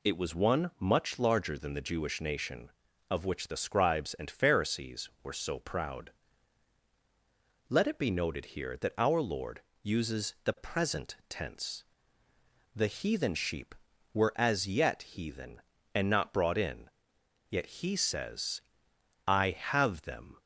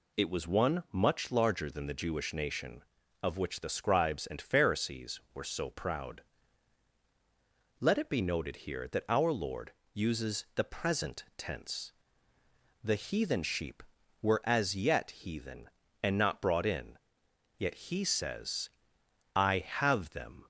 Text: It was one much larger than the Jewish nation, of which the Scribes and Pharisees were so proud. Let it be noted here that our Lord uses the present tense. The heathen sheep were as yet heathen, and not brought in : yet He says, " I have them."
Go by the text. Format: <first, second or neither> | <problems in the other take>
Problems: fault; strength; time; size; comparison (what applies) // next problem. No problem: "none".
neither | pauses between "Lord" and "uses"; slight; the same in both